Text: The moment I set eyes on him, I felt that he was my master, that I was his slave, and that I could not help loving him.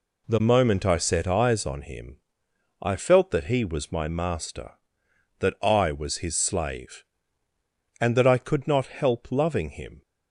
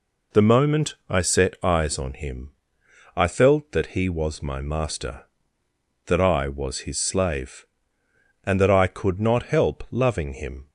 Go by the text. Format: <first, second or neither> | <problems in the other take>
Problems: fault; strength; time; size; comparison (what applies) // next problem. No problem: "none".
neither | none